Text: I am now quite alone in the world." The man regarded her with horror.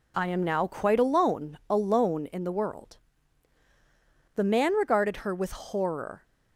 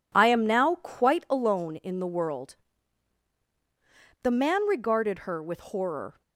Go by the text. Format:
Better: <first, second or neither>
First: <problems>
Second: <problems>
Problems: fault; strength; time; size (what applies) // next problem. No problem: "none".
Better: second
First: says "alone" twice; at 1.6 s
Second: none